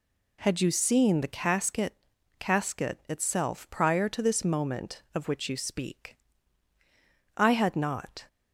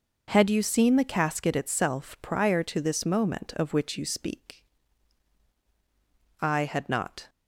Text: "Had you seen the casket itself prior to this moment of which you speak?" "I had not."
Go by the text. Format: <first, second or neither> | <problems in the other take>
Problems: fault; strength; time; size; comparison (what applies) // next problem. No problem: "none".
second | says "casket" twice; at 2.3 s